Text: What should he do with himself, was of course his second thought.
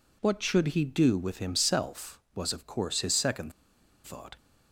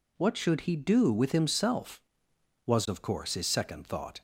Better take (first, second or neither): second